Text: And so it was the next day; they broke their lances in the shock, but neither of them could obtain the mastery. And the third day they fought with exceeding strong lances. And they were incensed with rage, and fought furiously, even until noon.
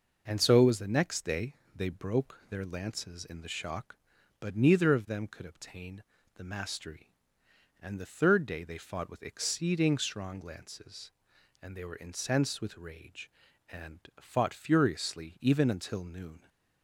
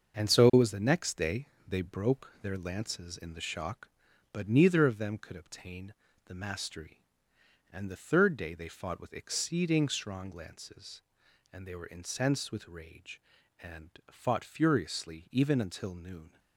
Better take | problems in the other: first | gets quieter; noticeable; throughout; 6 dB // pauses between "obtain" and "the"; slight; at 5.9 s; 0.34 s long; slight in the first // pauses between "and" and "fought"; slight; at 13.8 s; 0.22 s long; slight in the first

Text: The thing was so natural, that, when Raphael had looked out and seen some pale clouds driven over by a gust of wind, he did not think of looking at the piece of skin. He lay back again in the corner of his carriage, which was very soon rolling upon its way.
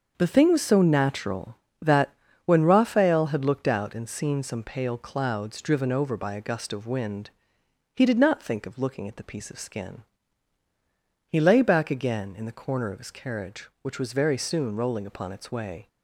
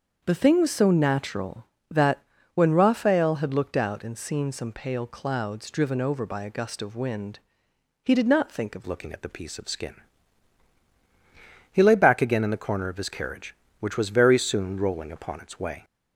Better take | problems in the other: first | starts louder than the rest; until 1.2 s; 6.5 dB; also in the first // changes voice at "looking"; from 8.8 s on; 7.0 s long

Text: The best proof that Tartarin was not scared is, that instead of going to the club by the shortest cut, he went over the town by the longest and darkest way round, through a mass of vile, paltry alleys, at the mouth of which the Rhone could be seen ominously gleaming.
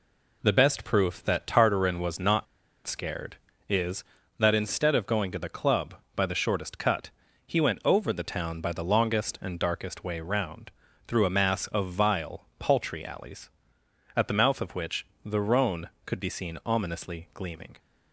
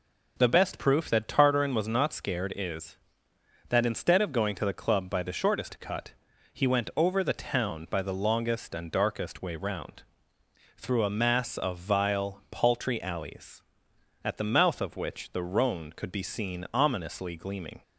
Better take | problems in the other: second | pauses between "not" and "scared"; at 2.4 s; 0.40 s long // pauses between "which" and "the"; slight; at 15.0 s; 0.20 s long

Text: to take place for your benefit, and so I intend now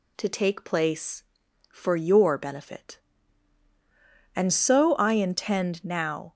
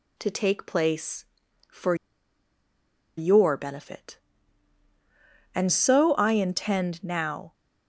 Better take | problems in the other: first | pauses between "for" and "your"; at 1.9 s; 1.2 s long

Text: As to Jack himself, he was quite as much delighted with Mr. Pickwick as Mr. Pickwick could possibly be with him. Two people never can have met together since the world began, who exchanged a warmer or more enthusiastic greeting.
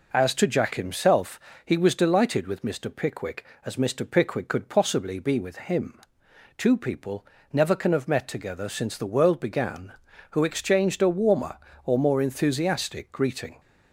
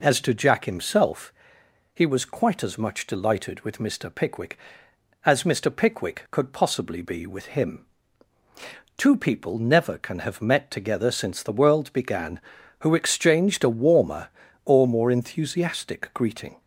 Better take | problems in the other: second | skips "quite as much"; at 1.9 s // pauses between "people" and "never"; slight; at 7.2 s; 0.28 s long

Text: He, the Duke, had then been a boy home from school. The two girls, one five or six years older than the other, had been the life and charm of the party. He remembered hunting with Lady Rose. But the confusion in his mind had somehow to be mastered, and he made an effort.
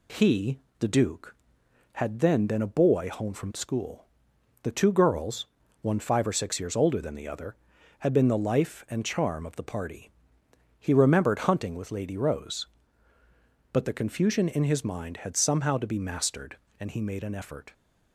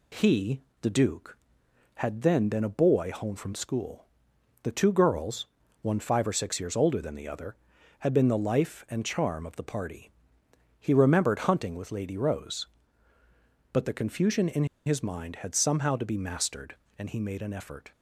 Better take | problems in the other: first | pauses between "in" and "his"; slight; at 14.6 s; 0.21 s long

